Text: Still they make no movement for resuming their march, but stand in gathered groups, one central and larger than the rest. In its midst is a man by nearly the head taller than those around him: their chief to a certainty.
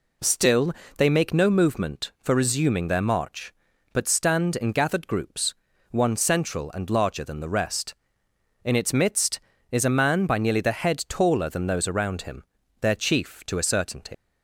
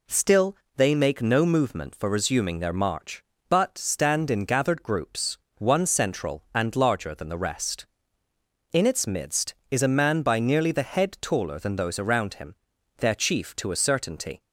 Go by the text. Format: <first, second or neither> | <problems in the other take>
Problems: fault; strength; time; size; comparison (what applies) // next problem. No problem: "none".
second | pauses between "Still" and "they"; slight; at 0.7 s; 0.24 s long; slight in the second // leaves "certainty" unfinished; at 14.1 s; 80 ms